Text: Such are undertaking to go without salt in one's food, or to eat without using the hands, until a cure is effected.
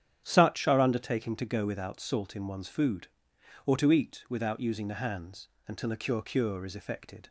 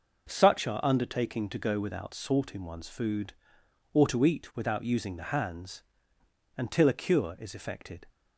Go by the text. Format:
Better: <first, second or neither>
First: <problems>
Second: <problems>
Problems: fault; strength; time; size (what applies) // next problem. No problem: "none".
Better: second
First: starts louder than the rest; strong; until 1.2 s; 9.5 dB // says "cure" twice; at 6.2 s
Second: none